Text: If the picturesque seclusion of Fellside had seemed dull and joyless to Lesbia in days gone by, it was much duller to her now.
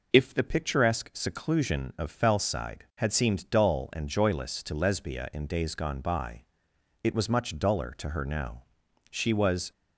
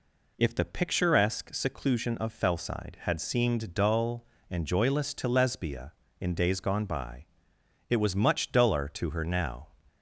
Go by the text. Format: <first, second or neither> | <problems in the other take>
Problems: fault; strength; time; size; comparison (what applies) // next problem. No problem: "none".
second | goes on to say "She was"; noticeable; from 9.0 s on; 0.62 s long